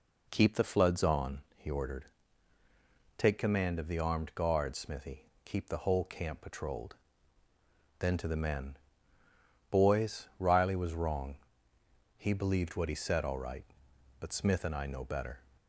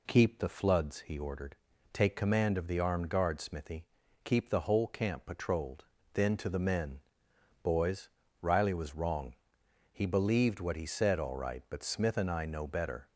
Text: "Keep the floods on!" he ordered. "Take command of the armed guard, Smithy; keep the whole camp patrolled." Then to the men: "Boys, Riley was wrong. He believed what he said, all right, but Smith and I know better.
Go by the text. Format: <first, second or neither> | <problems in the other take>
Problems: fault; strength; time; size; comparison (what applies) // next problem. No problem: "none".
first | skips "on"; at 1.0 s